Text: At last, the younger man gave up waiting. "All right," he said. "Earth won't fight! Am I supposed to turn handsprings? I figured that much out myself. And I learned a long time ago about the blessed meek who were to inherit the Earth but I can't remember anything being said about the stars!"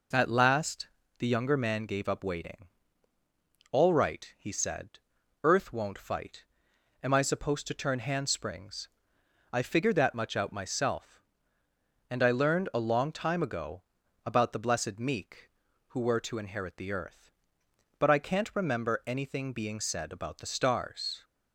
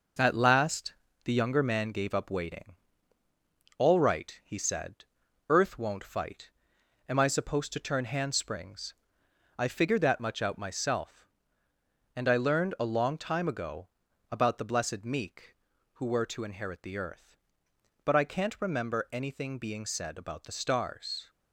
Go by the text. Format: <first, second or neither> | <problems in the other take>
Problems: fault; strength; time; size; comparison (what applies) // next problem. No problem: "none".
first | gets quieter; noticeable; throughout; 4 dB // pauses between "ago" and "about"; at 13.8 s; 0.44 s long; also in the first